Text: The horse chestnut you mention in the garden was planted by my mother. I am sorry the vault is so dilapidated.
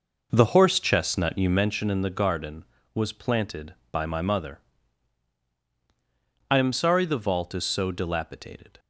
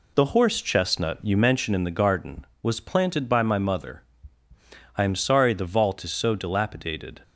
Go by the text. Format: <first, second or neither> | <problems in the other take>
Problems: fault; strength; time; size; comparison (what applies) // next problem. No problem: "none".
second | starts louder than the rest; noticeable; until 1.6 s; 5 dB